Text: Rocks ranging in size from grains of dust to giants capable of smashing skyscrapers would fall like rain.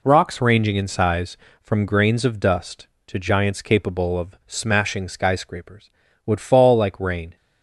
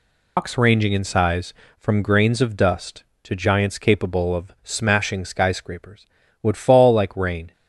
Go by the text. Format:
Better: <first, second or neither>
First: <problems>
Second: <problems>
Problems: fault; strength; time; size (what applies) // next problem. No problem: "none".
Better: first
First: none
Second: loses the start of "Rocks"; at 0.3 s; 170 ms